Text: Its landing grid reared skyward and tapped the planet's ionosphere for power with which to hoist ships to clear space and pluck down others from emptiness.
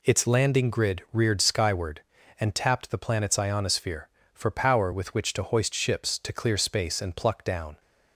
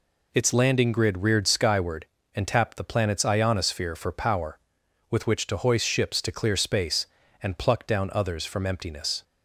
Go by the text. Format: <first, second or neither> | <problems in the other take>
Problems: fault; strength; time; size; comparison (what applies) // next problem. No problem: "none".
second | stops before "others from emptiness"; at 7.7 s